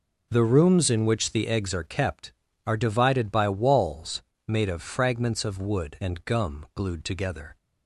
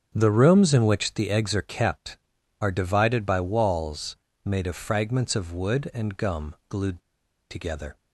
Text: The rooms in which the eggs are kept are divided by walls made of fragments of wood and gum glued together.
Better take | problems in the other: first | starts louder than the rest; strong; until 1.1 s; 7 dB // pauses between "walls" and "made"; slight; at 4.1 s; 0.30 s long; slight in the first // pauses between "gum" and "glued"; slight; at 6.5 s; 0.16 s long // pauses between "glued" and "together"; noticeable; at 7.0 s; 0.49 s long

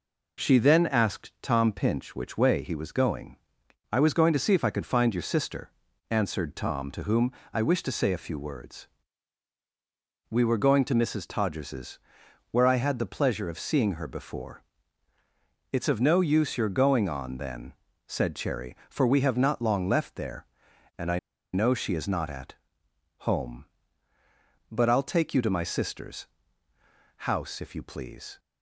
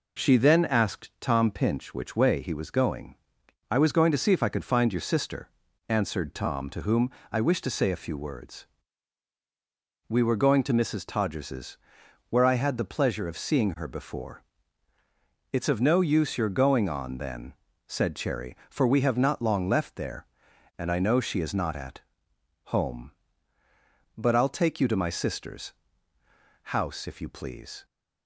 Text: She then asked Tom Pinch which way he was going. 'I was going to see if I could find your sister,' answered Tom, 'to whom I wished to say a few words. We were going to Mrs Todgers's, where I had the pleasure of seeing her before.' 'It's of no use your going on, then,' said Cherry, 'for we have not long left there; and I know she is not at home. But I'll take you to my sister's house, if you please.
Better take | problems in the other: second | pauses between "whom" and "I"; slight; at 7.3 s; 0.20 s long; slight in the second // pauses between "I" and "know"; slight; at 21.1 s; 0.34 s long // pauses between "at" and "home"; noticeable; at 22.5 s; 0.74 s long; noticeable in the second // pauses between "sister's" and "house"; noticeable; at 26.2 s; 0.92 s long; noticeable in the second

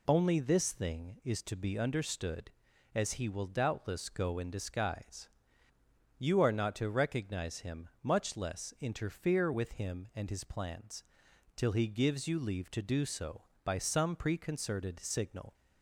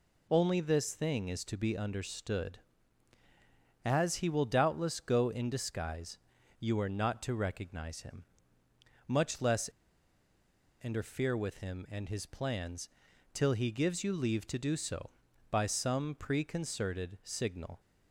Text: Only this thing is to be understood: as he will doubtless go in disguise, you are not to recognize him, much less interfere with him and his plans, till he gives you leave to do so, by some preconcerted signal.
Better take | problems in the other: first | pauses between "less" and "interfere"; at 9.6 s; 1.1 s long

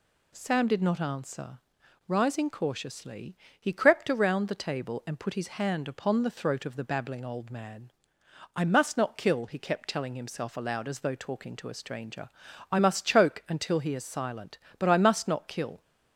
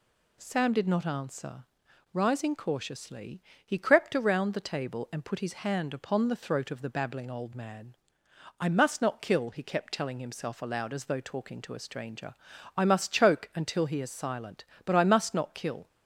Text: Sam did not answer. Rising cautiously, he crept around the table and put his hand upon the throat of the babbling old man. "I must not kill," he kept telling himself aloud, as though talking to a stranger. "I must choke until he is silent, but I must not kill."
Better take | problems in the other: neither | none

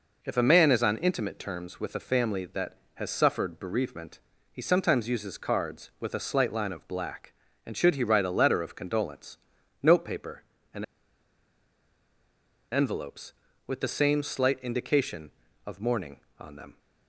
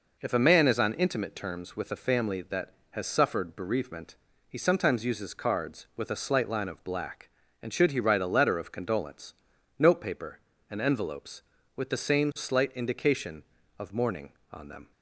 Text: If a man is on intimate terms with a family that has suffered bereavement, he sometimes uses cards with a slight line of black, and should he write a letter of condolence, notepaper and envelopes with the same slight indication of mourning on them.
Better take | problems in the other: second | pauses between "and" and "envelopes"; strong; at 10.8 s; 1.8 s long

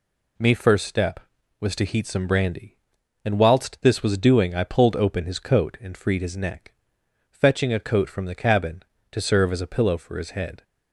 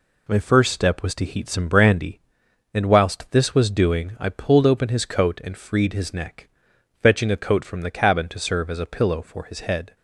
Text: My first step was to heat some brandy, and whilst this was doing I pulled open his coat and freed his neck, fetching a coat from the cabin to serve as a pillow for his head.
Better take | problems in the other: second | says "Me" for "My"; at 0.3 s

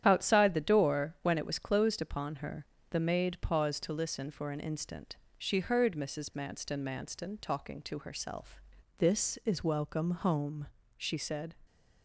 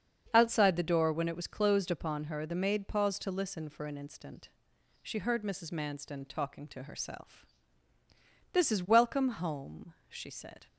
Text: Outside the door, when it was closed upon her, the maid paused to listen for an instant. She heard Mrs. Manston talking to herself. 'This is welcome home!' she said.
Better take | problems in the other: second | starts louder than the rest; strong; until 1.0 s; 9.5 dB; strong in the second // says "Manston" twice; at 6.8 s

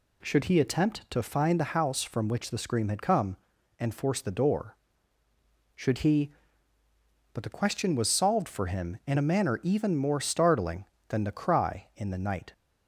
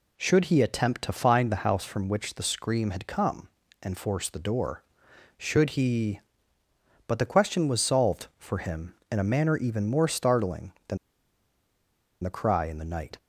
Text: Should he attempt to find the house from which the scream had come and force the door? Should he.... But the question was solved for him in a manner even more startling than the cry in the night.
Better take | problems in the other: first | pauses between "than" and "the"; strong; at 10.9 s; 1.2 s long

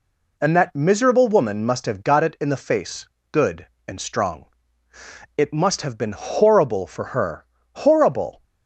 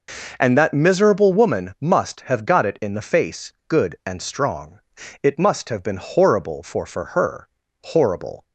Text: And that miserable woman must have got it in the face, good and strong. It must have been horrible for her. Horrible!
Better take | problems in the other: first | says "for" twice; at 6.8 s

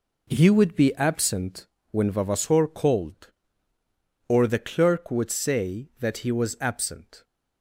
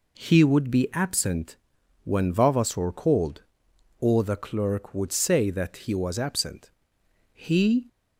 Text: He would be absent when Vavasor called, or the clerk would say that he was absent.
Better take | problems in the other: first | pauses between "absent" and "when"; noticeable; at 1.5 s; 0.48 s long; slight in the first // goes on to say "He"; from 7.3 s on; 0.54 s long

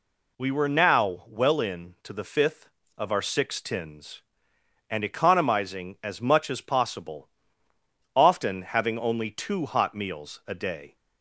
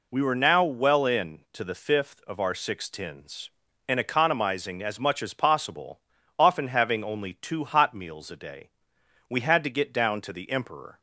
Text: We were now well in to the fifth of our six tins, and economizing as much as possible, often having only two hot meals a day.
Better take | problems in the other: first | goes on to say "We had to get down to the Emperor"; strong; from 9.2 s on; 1.7 s long

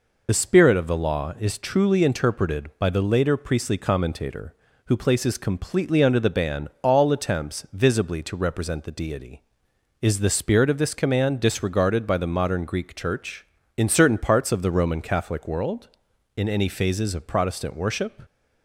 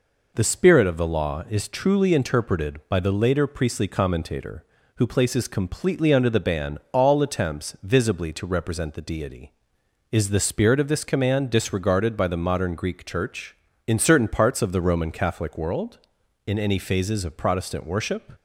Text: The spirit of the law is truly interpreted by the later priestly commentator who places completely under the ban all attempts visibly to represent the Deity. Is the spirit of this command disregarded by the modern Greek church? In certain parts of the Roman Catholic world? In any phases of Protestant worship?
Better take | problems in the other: second | loses the start of "The"; at 0.2 s; 40 ms // pauses between "ban" and "all"; slight; at 6.6 s; 0.16 s long; slight in the second

